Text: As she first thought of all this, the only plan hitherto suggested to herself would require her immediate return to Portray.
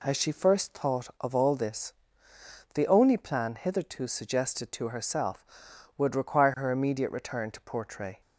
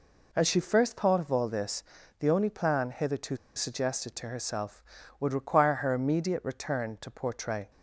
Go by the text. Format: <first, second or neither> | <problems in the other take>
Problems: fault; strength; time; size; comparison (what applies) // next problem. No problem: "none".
first | pauses between "hitherto" and "suggested"; slight; at 3.3 s; 0.20 s long